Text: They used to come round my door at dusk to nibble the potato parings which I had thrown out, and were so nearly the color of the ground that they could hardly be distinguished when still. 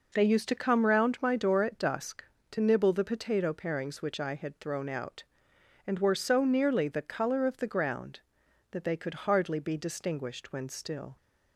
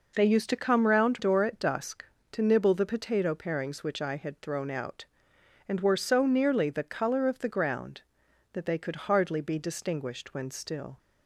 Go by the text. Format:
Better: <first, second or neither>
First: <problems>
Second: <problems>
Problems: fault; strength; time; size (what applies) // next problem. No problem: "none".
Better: first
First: none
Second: skips "my"; at 1.1 s